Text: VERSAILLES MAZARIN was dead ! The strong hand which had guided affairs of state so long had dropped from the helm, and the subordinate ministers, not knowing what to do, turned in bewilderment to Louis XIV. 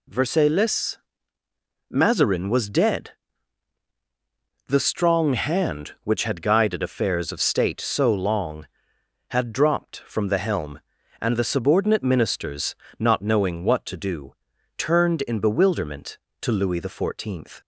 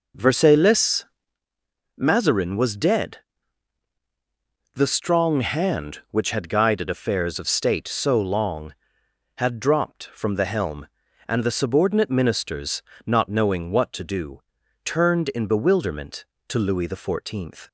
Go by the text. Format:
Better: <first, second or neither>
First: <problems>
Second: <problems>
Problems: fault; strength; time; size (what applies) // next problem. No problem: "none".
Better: first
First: pauses between "VERSAILLES" and "MAZARIN"; noticeable; at 0.9 s; 0.94 s long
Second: starts louder than the rest; noticeable; until 1.4 s; 5 dB // pauses between "VERSAILLES" and "MAZARIN"; noticeable; at 1.0 s; 0.94 s long